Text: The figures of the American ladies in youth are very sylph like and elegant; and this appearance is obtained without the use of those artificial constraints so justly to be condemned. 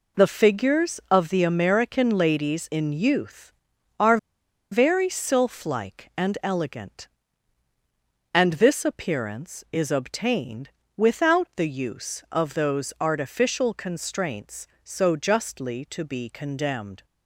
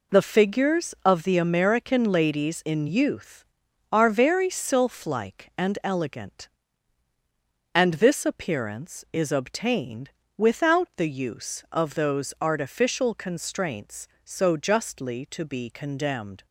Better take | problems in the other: second | pauses between "are" and "very"; noticeable; at 4.1 s; 0.54 s long // pauses between "obtained" and "without"; slight; at 10.7 s; 0.26 s long; slight in the second

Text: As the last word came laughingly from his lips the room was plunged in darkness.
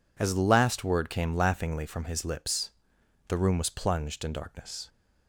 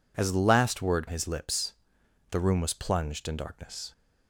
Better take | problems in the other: first | skips "came laughingly from"; at 1.0 s // pauses between "lips" and "the"; noticeable; at 1.7 s; 0.56 s long; noticeable in the first

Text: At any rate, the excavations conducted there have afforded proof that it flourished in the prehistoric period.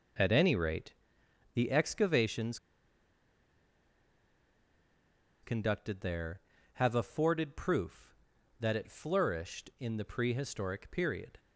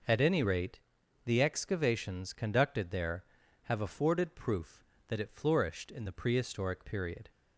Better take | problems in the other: second | pauses between "excavations" and "conducted"; strong; at 2.5 s; 2.8 s long

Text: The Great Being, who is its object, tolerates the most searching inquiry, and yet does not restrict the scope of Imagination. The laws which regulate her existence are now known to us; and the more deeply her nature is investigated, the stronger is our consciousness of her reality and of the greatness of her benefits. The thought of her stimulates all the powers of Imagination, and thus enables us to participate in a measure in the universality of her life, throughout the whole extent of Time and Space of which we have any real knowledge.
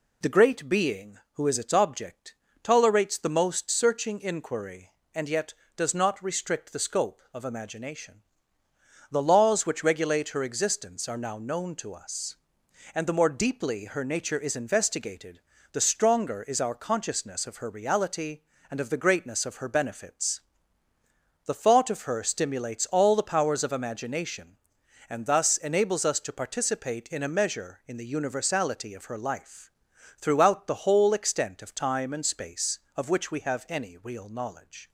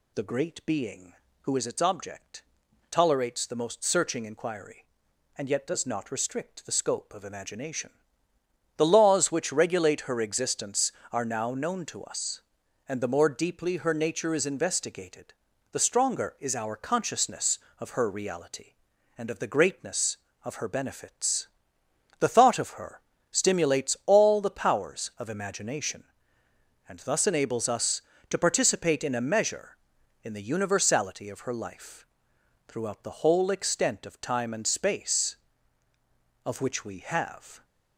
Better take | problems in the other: first | pauses between "her" and "stimulates"; slight; at 23.0 s; 0.32 s long // stops before "any real knowledge"; at 37.6 s

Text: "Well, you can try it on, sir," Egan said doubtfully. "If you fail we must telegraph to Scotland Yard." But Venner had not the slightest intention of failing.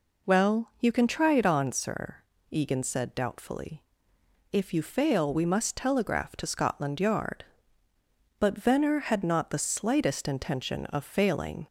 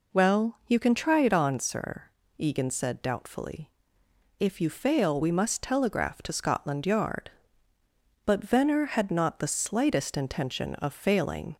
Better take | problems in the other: neither | none

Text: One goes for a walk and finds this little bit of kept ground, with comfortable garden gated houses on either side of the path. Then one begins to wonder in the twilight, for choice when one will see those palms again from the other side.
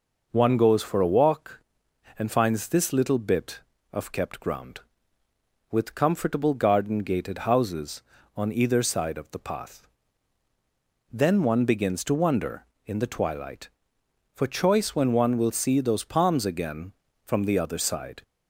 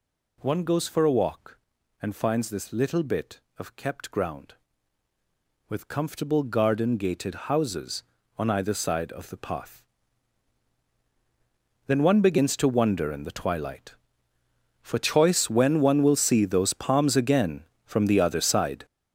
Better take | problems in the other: first | gets louder; strong; throughout; 10 dB // pauses between "gated" and "houses"; slight; at 7.3 s; 0.16 s long

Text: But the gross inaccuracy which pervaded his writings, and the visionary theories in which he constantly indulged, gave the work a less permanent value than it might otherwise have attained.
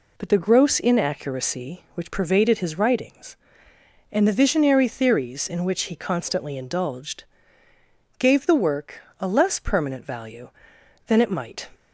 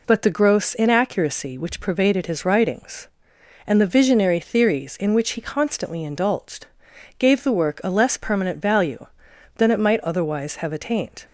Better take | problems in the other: second | pauses between "work" and "a"; slight; at 8.9 s; 0.20 s long // stops before "otherwise have attained"; at 11.7 s

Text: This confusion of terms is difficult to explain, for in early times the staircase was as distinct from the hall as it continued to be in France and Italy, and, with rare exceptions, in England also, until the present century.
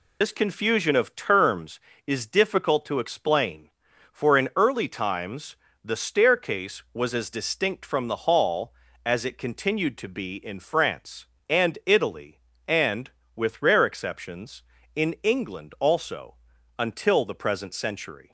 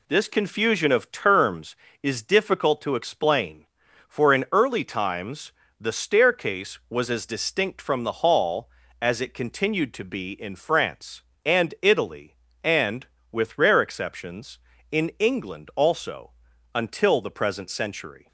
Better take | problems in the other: second | loses the start of "This"; at 0.2 s; 95 ms // pauses between "times" and "the"; slight; at 5.5 s; 0.30 s long; slight in the second

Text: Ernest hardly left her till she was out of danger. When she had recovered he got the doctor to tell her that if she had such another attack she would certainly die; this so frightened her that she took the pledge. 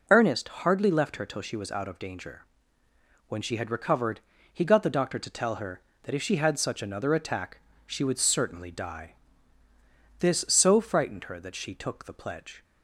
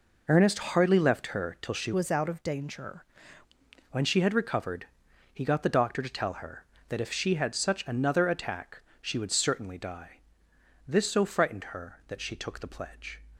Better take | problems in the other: first | changes voice from "was" to "danger"; from 1.9 to 3.0 s; 1.1 s long // pauses between "recovered" and "he"; noticeable; at 4.8 s; 0.46 s long; slight in the first // pauses between "attack" and "she"; slight; at 8.8 s; 0.18 s long; slight in the first

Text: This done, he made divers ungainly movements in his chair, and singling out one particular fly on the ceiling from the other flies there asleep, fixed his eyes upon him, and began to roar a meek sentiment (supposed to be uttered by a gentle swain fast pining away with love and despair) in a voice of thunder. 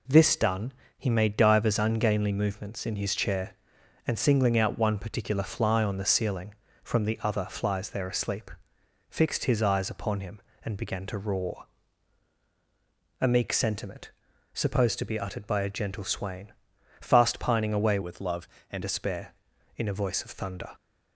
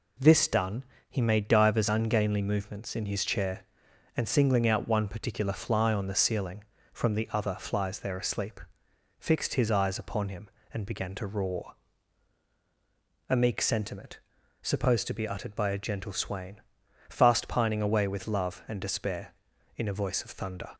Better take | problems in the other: second | pauses between "roar" and "a"; strong; at 11.6 s; 1.5 s long; strong in the second // pauses between "swain" and "fast"; noticeable; at 16.5 s; 0.48 s long; noticeable in the second // changes voice from "with" to "and"; from 18.0 to 18.8 s; 0.8 s long

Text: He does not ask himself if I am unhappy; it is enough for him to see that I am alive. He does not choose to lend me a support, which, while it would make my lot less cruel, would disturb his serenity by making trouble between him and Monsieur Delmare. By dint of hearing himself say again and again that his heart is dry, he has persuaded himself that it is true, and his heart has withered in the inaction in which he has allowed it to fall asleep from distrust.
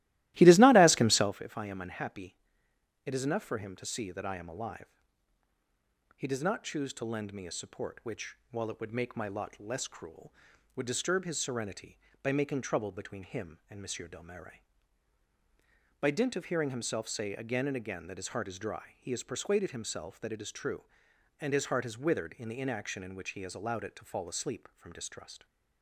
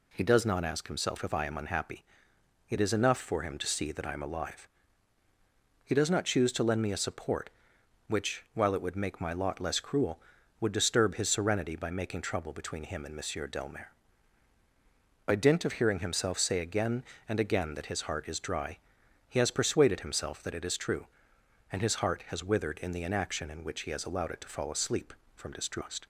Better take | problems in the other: second | starts louder than the rest; strong; until 1.3 s; 16.5 dB

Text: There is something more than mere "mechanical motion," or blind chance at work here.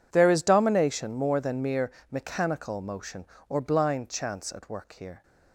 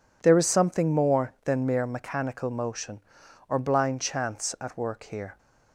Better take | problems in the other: second | says "domination" for "something"; at 0.4 s // pauses between "mere" and "mechanical"; slight; at 1.8 s; 0.22 s long

